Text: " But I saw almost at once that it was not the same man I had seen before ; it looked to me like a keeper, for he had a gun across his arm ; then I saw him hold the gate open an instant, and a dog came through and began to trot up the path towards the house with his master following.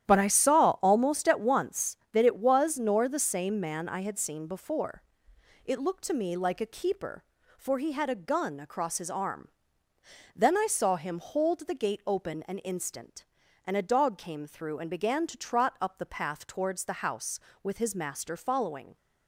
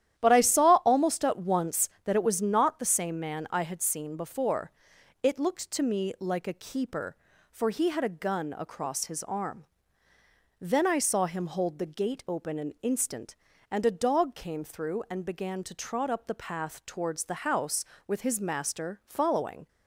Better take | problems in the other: second | starts louder than the rest; strong; until 1.1 s; 11 dB; strong in the second // says "nor" for "not"; at 2.7 s

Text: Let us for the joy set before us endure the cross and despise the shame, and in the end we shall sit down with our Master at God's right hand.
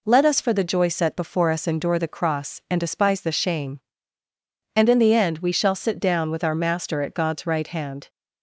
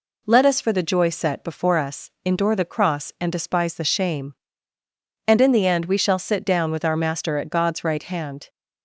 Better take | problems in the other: neither | none

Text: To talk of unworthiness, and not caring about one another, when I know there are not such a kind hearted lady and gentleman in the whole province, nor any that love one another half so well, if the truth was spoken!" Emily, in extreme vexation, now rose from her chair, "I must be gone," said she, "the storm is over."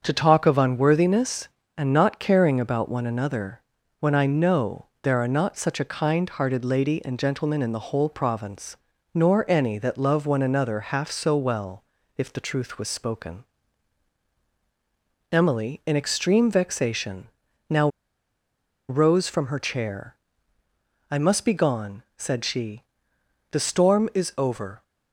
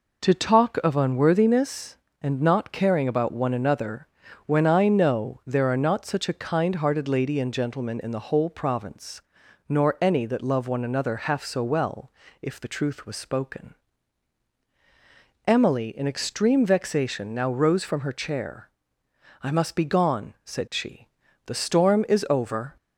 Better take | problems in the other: second | starts louder than the rest; until 1.0 s; 6.5 dB // pauses between "know" and "there"; slight; at 4.8 s; 0.16 s long // pauses between "now" and "rose"; at 17.8 s; 1.0 s long

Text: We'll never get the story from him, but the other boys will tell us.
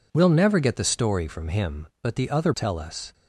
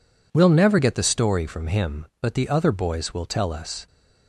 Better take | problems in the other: second | skips "boys will"; at 2.5 s

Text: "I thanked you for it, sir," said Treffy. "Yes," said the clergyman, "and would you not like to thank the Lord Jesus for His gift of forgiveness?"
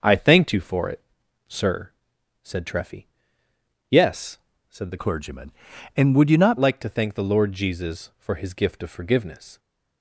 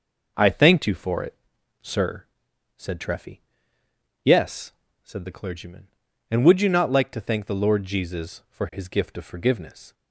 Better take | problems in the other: second | changes voice from "clergyman" to "not"; from 4.9 to 6.5 s; 1.6 s long

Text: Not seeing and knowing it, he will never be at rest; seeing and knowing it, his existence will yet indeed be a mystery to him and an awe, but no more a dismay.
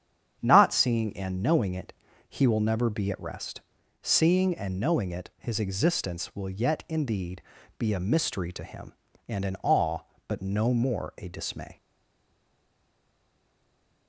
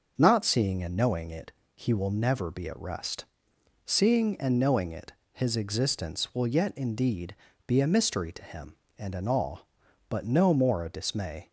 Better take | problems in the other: second | starts louder than the rest; strong; until 1.4 s; 8.5 dB; also in the second // pauses between "indeed" and "be"; slight; at 7.4 s; 0.36 s long; slight in the second // stays silent after the last word; from 11.7 s on; 2.3 s long

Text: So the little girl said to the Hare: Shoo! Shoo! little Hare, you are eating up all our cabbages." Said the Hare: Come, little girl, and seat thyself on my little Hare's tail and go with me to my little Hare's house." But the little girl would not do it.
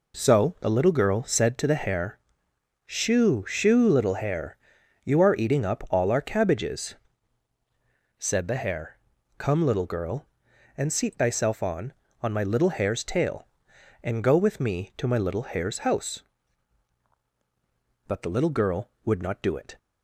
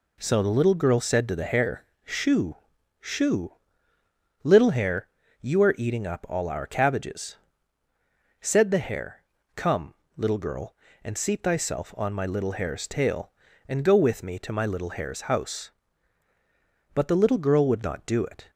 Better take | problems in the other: second | says "on" twice; at 12.2 s

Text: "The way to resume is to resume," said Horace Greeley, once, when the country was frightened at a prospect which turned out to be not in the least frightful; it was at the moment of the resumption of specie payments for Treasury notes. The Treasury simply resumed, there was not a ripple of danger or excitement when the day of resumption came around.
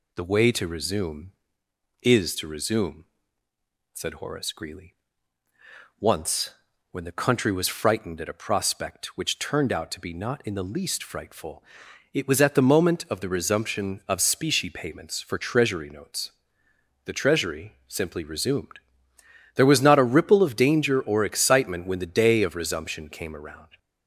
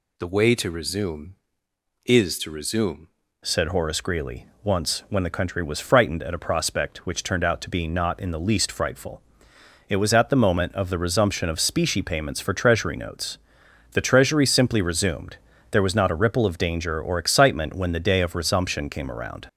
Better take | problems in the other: first | changes voice at "said"; from 3.4 s on; 16.0 s long

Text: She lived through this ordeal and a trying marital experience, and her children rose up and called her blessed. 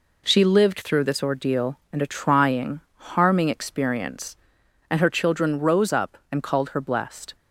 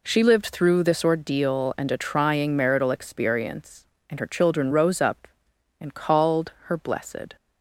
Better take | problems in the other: second | says "harming" for "marital"; at 3.1 s

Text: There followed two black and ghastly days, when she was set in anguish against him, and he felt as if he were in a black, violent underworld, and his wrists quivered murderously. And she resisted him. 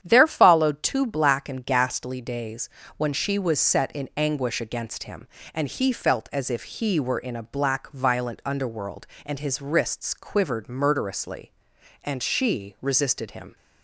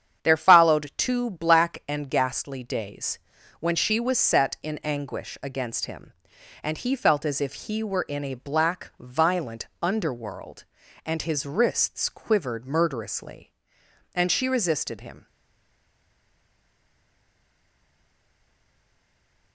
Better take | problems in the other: first | starts louder than the rest; strong; until 1.2 s; 8.5 dB; strong in the first // pauses between "violent" and "underworld"; slight; at 9.6 s; 0.16 s long // stays silent after the last word; strong; from 15.2 s on; 4.3 s long

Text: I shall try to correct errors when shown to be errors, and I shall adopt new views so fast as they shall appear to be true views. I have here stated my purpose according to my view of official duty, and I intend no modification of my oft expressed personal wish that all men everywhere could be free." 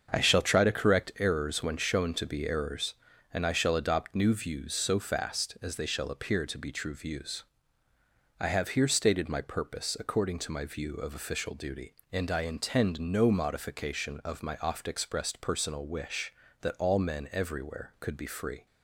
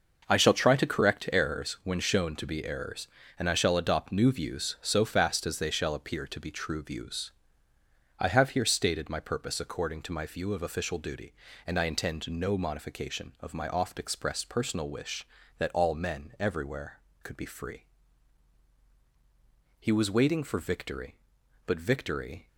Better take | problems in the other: first | starts louder than the rest; until 1.3 s; 6 dB; also in the first // goes on to say "He was waiting for victory but victory"; strong; from 19.7 s on; 2.6 s long

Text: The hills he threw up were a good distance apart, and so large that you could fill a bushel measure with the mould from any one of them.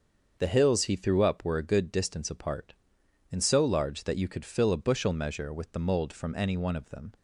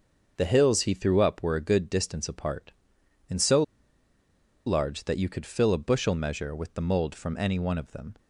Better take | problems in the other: first | starts louder than the rest; until 1.4 s; 6.5 dB; also in the first // pauses between "so" and "large"; at 3.6 s; 1.0 s long

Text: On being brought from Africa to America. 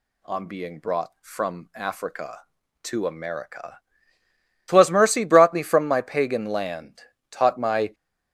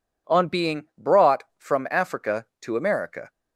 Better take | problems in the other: second | goes on to say "TWAS mercy brought me from my Pagan land Taught my"; strong; from 4.6 s on; 3.2 s long

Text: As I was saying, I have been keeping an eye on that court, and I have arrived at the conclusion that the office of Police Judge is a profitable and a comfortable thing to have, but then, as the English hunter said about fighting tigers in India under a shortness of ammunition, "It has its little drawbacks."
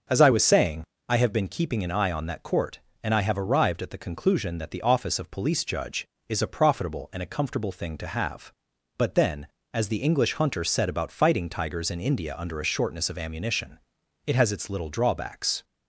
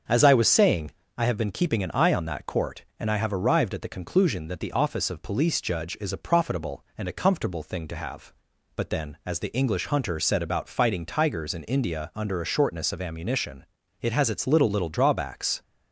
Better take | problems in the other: first | starts louder than the rest; until 1.3 s; 7 dB; also in the first // says "little" twice; at 14.6 s

